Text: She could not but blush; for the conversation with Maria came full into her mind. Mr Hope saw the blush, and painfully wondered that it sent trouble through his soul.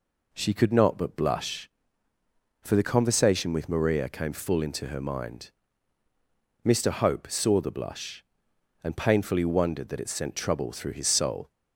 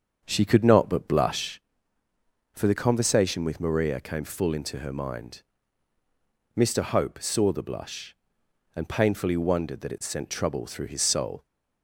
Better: first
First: none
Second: starts louder than the rest; strong; until 1.7 s; 7.5 dB

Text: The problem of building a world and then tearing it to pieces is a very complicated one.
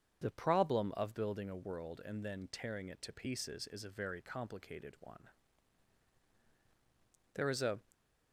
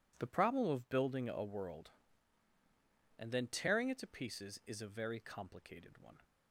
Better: second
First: starts louder than the rest; until 1.2 s; 7 dB // goes on to say "There is a"; slight; from 7.3 s on; 0.46 s long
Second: none

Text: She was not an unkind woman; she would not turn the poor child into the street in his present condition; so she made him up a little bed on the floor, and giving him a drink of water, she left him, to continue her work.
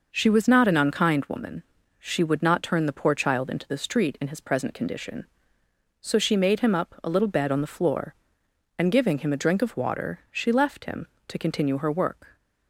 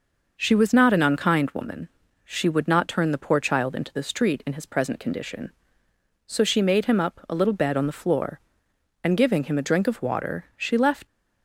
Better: first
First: none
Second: stops before "him to continue her work"; at 11.0 s

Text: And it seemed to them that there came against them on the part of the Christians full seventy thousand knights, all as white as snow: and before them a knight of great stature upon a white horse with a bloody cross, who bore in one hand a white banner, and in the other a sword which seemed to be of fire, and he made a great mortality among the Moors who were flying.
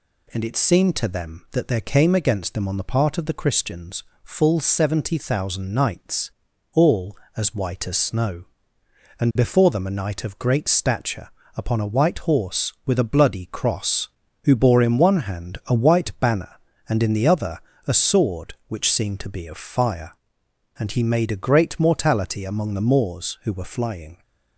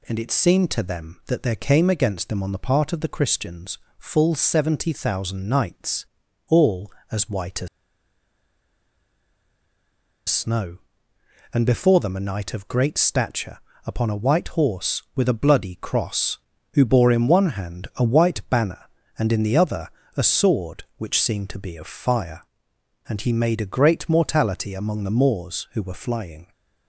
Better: first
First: pauses between "Christians" and "full"; slight; at 4.0 s; 0.20 s long // pauses between "stature" and "upon"; slight; at 11.2 s; 0.26 s long // pauses between "other" and "a"; slight; at 17.5 s; 0.28 s long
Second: pauses between "Christians" and "full"; slight; at 3.7 s; 0.20 s long // pauses between "as" and "snow"; strong; at 7.6 s; 2.6 s long // pauses between "stature" and "upon"; slight; at 13.5 s; 0.26 s long // pauses between "other" and "a"; slight; at 19.8 s; 0.28 s long

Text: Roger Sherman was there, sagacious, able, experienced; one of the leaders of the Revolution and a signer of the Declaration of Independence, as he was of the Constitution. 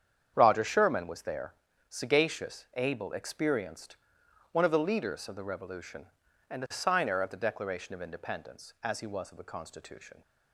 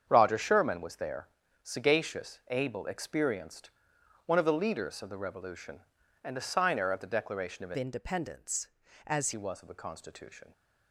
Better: first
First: starts louder than the rest; strong; until 1.3 s; 8 dB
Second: starts louder than the rest; strong; until 1.1 s; 7.5 dB // changes voice from "Independence" to "as"; from 7.7 to 9.3 s; 1.6 s long

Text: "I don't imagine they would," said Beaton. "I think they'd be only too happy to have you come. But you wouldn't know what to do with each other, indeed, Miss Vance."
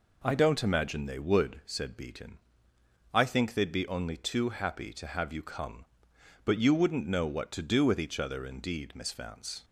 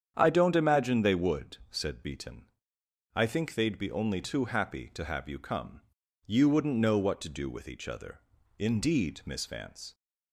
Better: first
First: none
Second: starts louder than the rest; strong; until 1.1 s; 8.5 dB // skips "But"; at 6.0 s

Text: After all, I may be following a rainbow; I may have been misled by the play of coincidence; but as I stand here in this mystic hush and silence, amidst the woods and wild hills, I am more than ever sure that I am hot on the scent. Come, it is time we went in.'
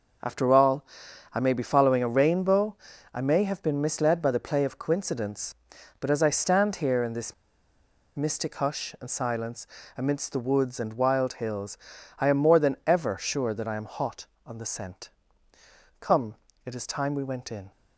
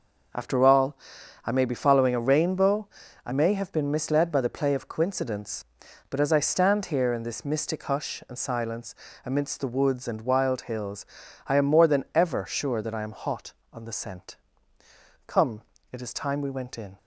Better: second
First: pauses between "this" and "mystic"; noticeable; at 7.3 s; 0.84 s long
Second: none

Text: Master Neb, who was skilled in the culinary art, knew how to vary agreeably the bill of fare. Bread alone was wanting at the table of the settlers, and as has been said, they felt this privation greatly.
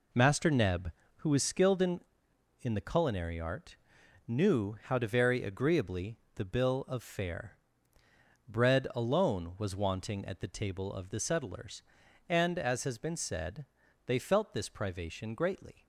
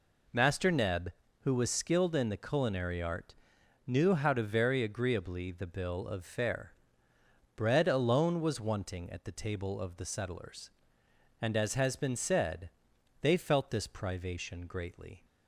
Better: second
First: says "in" twice; at 2.6 s // pauses between "agreeably" and "the"; slight; at 6.1 s; 0.16 s long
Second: none

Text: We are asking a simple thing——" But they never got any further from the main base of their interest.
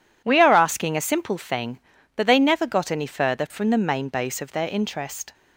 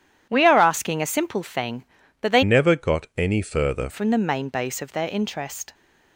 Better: first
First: none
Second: changes voice from "never" to "further"; from 2.4 to 3.8 s; 1.4 s long

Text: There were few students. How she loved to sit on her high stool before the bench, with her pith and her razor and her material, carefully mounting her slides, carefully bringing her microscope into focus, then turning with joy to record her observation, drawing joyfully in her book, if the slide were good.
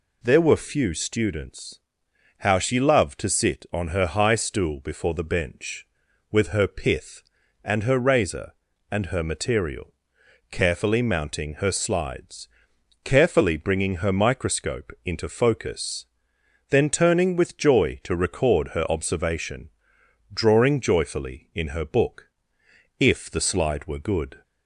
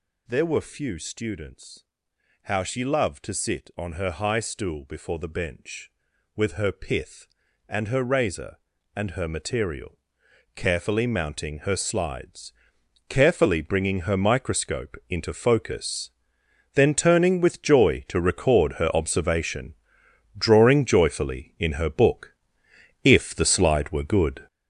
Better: first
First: none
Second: gets louder; strong; throughout; 8 dB

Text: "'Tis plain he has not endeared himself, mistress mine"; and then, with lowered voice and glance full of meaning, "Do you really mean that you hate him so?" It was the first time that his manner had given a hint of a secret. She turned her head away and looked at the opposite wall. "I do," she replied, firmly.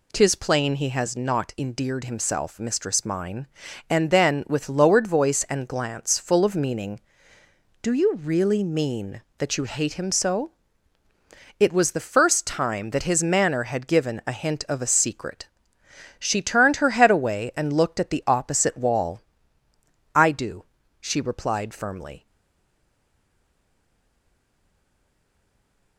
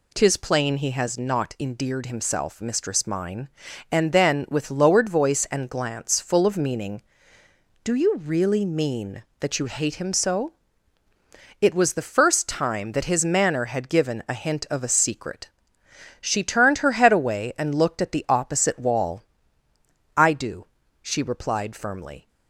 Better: second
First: stays silent after the last word; strong; from 22.2 s on; 3.7 s long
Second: none

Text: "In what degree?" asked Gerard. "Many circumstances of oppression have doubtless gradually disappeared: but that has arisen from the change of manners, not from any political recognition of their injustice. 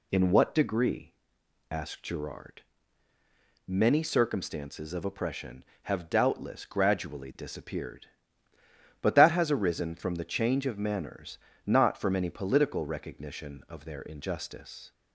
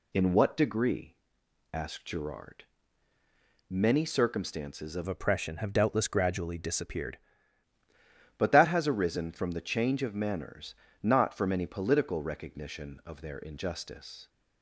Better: first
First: none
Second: changes voice from "oppression" to "disappeared"; from 5.0 to 7.1 s; 2.1 s long

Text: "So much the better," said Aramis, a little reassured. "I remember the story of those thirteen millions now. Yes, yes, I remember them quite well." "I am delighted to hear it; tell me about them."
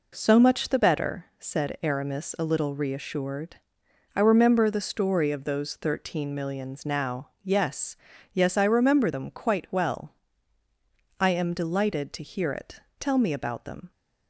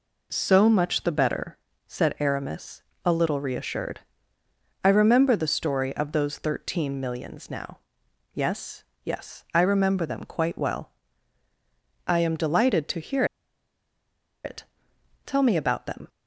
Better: first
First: none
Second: pauses between "hear" and "it"; at 13.2 s; 1.1 s long

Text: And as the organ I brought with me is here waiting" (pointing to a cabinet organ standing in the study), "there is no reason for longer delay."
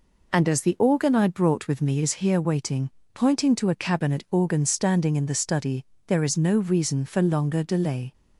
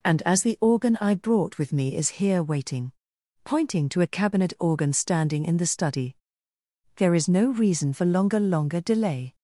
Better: first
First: none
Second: says "longer" twice; at 8.3 s

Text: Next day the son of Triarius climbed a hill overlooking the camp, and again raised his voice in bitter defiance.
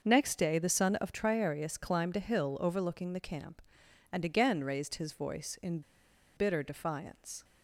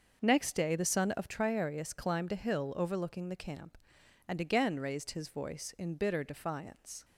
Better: second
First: starts louder than the rest; until 1.0 s; 6.5 dB // pauses between "in" and "bitter"; noticeable; at 5.8 s; 0.56 s long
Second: starts louder than the rest; until 1.2 s; 6 dB

